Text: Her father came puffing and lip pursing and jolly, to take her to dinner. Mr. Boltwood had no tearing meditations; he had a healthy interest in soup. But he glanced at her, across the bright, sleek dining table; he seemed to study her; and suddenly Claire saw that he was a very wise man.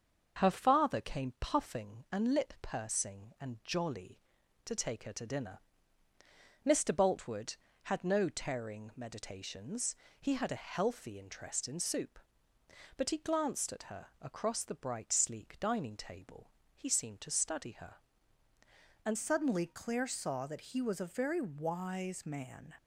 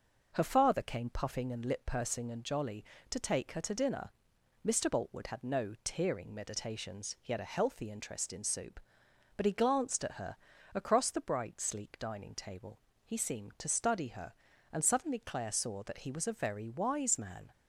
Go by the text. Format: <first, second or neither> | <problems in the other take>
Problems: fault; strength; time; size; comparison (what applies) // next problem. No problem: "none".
second | starts louder than the rest; until 1.4 s; 6.5 dB // changes voice at "suddenly"; from 19.1 s on; 3.6 s long